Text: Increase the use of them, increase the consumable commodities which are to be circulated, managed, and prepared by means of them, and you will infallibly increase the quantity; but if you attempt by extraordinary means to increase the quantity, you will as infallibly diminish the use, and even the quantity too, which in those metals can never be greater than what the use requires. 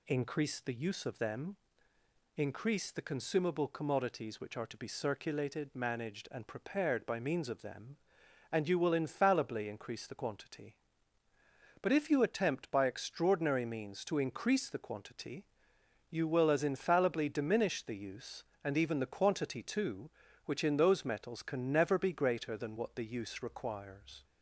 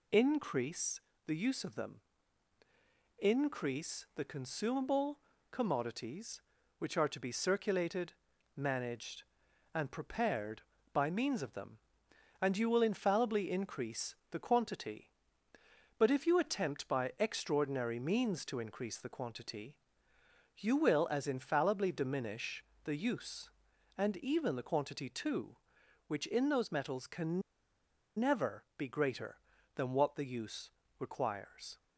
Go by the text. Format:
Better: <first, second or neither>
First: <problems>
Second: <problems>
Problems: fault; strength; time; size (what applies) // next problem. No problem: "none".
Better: first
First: none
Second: pauses between "Increase" and "the"; slight; at 1.0 s; 0.26 s long // pauses between "consumable" and "commodities"; slight; at 5.1 s; 0.32 s long // pauses between "increase" and "the"; slight; at 14.1 s; 0.16 s long // pauses between "diminish" and "the"; slight; at 22.6 s; 0.22 s long // pauses between "can" and "never"; noticeable; at 27.4 s; 0.77 s long // pauses between "never" and "be"; slight; at 28.6 s; 0.16 s long // pauses between "use" and "requires"; slight; at 30.6 s; 0.30 s long